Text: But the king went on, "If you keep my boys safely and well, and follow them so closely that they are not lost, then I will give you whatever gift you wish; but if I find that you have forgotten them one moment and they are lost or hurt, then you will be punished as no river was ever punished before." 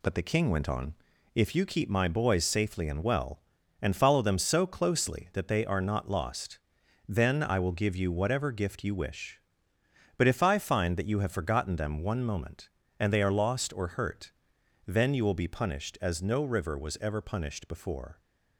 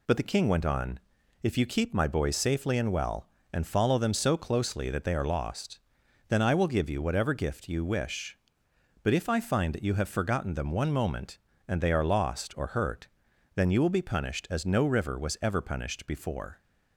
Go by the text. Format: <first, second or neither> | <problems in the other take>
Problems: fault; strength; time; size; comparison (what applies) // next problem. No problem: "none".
first | skips "not"; at 5.2 s